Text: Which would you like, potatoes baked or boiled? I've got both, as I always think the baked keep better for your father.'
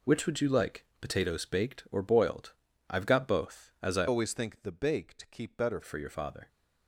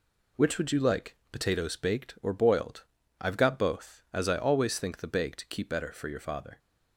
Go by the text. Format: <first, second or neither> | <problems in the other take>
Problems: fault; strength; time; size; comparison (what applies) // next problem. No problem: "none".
second | changes voice from "always" to "better"; from 4.0 to 5.8 s; 1.8 s long